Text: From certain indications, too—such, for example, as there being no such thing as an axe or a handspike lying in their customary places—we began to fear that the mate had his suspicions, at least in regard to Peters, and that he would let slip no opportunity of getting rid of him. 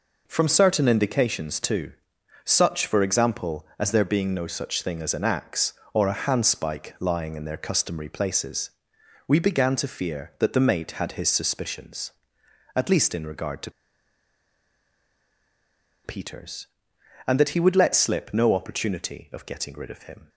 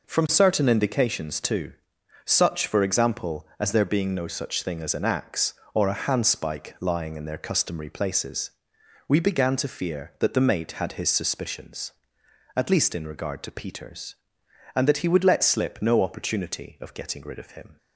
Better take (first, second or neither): second